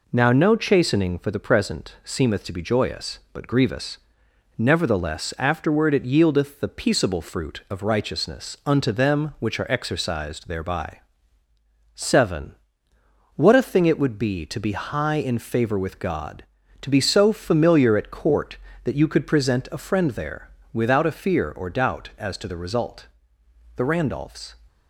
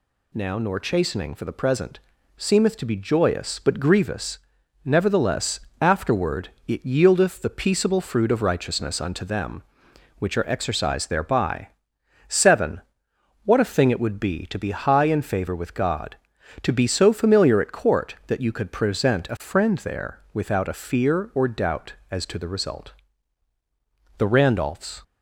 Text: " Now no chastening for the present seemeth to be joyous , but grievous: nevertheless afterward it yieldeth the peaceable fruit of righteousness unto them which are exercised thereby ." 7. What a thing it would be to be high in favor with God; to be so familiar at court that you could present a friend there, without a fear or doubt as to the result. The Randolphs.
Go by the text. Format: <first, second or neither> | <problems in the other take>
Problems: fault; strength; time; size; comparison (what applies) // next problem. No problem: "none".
first | says "nor" for "no"; at 0.5 s // pauses between "present" and "seemeth"; at 1.9 s; 0.38 s long // pauses between "nevertheless" and "afterward"; slight; at 5.5 s; 0.20 s long // pauses between "afterward" and "it"; slight; at 6.4 s; 0.18 s long